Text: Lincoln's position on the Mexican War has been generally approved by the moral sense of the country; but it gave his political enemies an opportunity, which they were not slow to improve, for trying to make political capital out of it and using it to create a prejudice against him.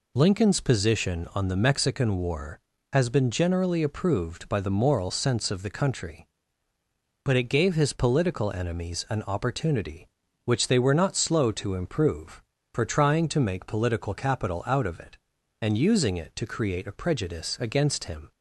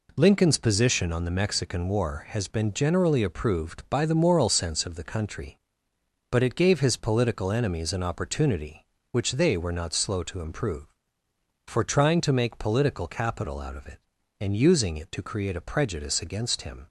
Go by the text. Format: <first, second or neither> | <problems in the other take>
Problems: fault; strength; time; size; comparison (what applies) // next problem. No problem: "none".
neither | none